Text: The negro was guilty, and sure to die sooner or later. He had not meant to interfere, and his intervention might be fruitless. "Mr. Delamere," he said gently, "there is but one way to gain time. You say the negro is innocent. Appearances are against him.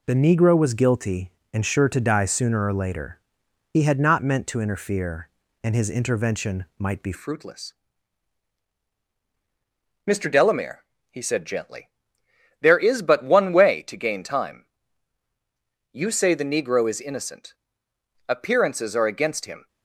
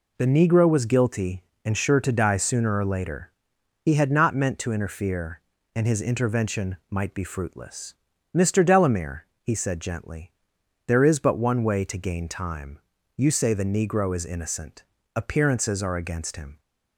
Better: second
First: changes voice at "fruitless"; from 7.1 s on; 12.5 s long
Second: none

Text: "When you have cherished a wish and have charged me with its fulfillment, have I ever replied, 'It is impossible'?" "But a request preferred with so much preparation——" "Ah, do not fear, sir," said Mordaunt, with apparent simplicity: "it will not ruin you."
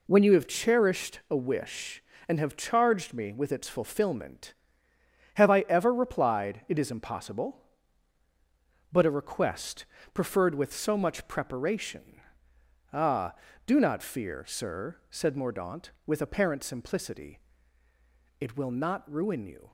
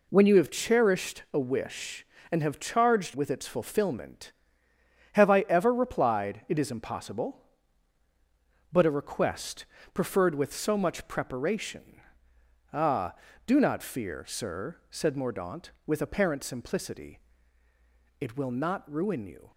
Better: first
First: pauses between "request" and "preferred"; slight; at 9.8 s; 0.28 s long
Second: skips "me"; at 3.1 s // pauses between "request" and "preferred"; slight; at 9.6 s; 0.28 s long

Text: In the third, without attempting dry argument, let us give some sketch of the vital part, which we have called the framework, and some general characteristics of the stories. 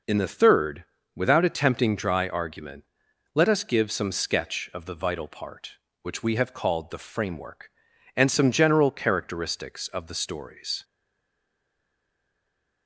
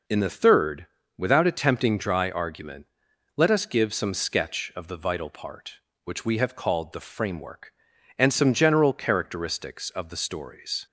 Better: second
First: stays silent after the last word; noticeable; from 10.8 s on; 2.0 s long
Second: none

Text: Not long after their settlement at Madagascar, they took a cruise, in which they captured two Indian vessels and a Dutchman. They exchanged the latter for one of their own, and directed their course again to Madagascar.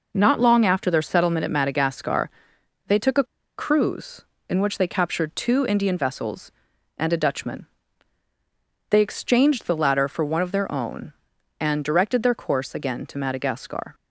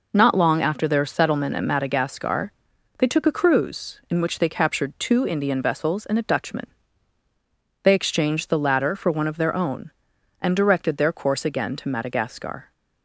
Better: second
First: pauses between "a" and "cruise"; slight; at 3.2 s; 0.34 s long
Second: none

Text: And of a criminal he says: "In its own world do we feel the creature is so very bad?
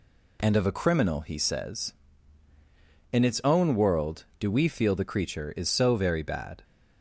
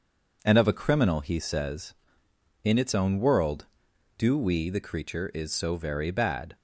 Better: first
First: none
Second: skips "feel"; at 4.6 s

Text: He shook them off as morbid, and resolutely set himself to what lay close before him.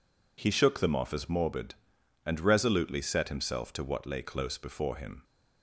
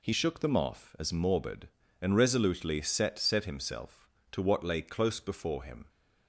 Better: first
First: none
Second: says "set" twice; at 3.1 s

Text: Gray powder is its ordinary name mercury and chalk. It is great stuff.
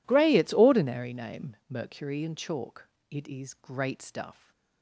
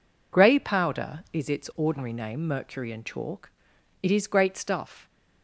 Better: second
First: skips "powder is"; at 0.3 s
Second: none

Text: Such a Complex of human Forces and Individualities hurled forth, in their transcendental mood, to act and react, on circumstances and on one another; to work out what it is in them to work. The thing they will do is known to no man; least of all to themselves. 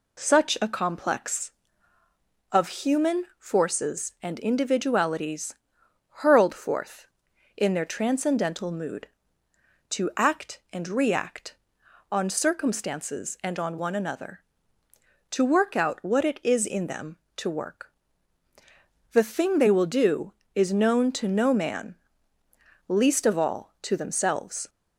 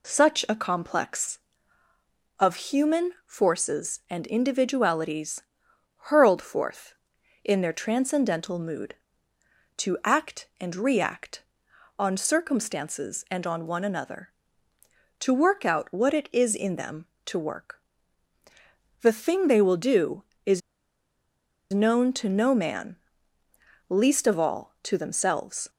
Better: first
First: pauses between "Individualities" and "hurled"; noticeable; at 5.5 s; 0.54 s long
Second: pauses between "Individualities" and "hurled"; noticeable; at 5.4 s; 0.54 s long // pauses between "is" and "known"; at 20.6 s; 1.1 s long

